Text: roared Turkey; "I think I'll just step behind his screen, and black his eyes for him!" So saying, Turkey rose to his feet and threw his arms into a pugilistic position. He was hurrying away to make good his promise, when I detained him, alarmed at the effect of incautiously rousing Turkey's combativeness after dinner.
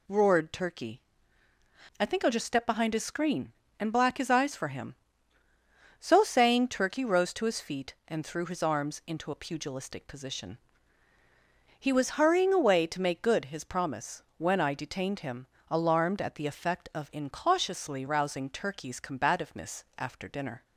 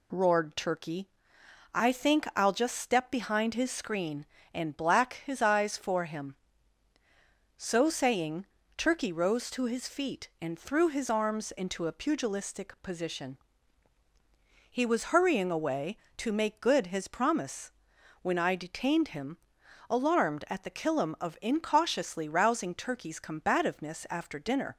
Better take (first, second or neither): first